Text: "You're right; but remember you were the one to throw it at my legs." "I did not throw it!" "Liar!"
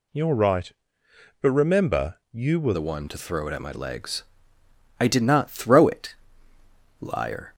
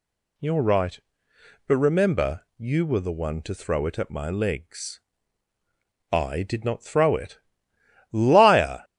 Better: second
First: changes voice at "the"; from 2.7 s on; 4.8 s long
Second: none

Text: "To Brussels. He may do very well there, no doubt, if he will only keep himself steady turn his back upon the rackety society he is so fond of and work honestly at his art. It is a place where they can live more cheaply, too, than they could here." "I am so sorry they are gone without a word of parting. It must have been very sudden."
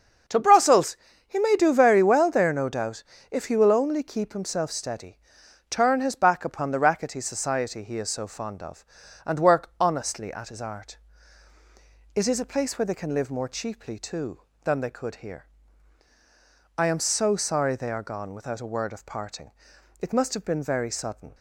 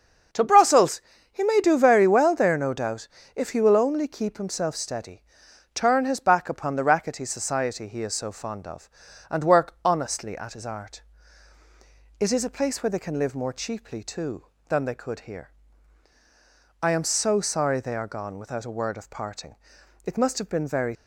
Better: first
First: starts louder than the rest; until 1.6 s; 6.5 dB // pauses between "steady" and "turn"; noticeable; at 5.1 s; 0.52 s long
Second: starts louder than the rest; until 1.6 s; 6.5 dB // pauses between "steady" and "turn"; noticeable; at 5.2 s; 0.52 s long // stops before "sudden"; at 20.9 s

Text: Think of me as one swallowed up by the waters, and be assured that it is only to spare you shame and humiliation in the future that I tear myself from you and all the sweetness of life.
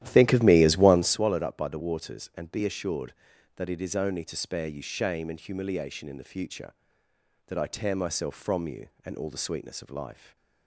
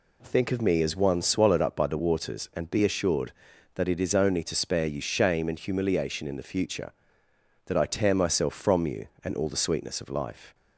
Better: second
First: starts louder than the rest; strong; until 1.2 s; 12.5 dB // stays silent after the last word; slight; from 10.1 s on; 0.5 s long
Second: none

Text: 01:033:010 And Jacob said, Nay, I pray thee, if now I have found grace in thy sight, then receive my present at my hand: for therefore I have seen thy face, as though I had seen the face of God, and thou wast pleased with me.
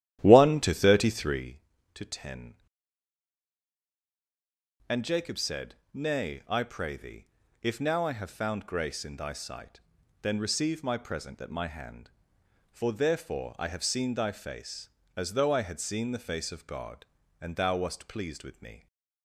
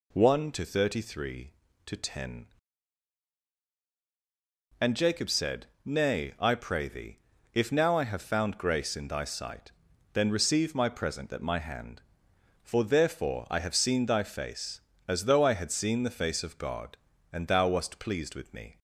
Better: second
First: starts louder than the rest; strong; until 1.5 s; 12.5 dB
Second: none

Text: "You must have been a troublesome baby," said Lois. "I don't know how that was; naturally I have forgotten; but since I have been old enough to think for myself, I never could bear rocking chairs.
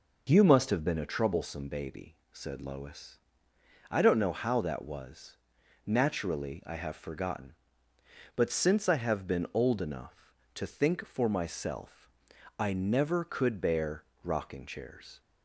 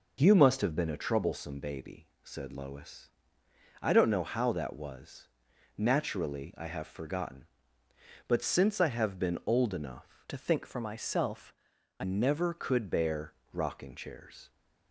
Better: first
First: pauses between "bear" and "rocking"; slight; at 14.0 s; 0.22 s long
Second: changes voice from "to" to "I"; from 10.2 to 12.0 s; 1.8 s long // pauses between "bear" and "rocking"; slight; at 13.3 s; 0.22 s long

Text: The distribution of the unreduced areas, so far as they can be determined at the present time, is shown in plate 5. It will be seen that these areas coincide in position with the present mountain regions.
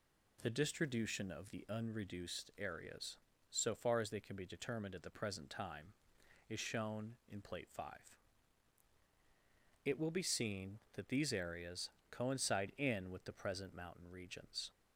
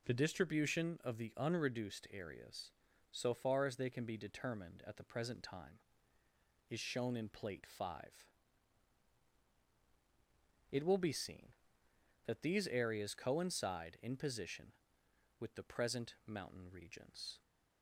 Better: second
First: pauses between "areas" and "coincide"; slight; at 11.8 s; 0.22 s long // skips "position"; at 13.0 s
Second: none

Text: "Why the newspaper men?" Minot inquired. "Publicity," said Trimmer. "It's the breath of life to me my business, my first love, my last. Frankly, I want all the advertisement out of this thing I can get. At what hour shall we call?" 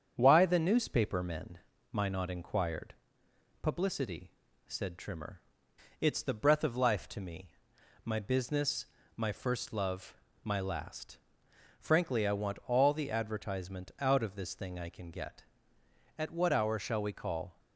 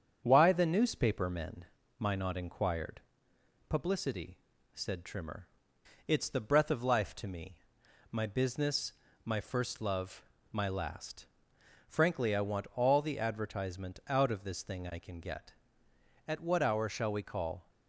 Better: neither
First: starts louder than the rest; strong; until 1.1 s; 7.5 dB // pauses between "me" and "my"; noticeable; at 7.5 s; 0.52 s long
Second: starts louder than the rest; strong; until 1.2 s; 7.5 dB // pauses between "me" and "my"; noticeable; at 7.5 s; 0.52 s long

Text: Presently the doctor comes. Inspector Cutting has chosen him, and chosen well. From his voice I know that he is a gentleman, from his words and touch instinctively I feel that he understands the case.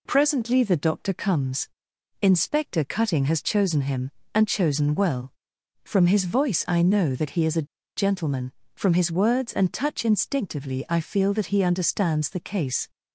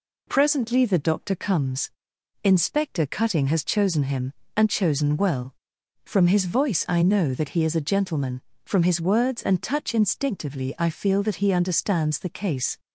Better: second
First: pauses between "a" and "gentleman"; slight; at 7.6 s; 0.30 s long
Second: none

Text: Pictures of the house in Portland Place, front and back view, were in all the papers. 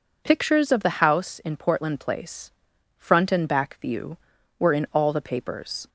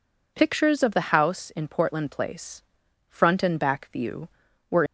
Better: first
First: none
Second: stops before "in all the papers"; at 4.8 s

